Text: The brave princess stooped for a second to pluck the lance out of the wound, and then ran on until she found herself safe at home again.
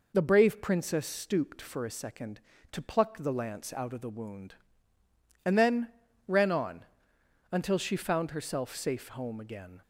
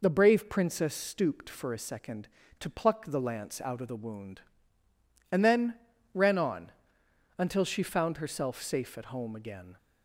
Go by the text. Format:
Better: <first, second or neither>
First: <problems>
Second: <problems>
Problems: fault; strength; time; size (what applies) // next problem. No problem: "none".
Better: second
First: pauses between "then" and "ran"; at 5.8 s; 0.38 s long // pauses between "on" and "until"; noticeable; at 6.8 s; 0.66 s long // skips "at"; at 9.1 s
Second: pauses between "then" and "ran"; at 5.7 s; 0.38 s long // pauses between "on" and "until"; noticeable; at 6.7 s; 0.66 s long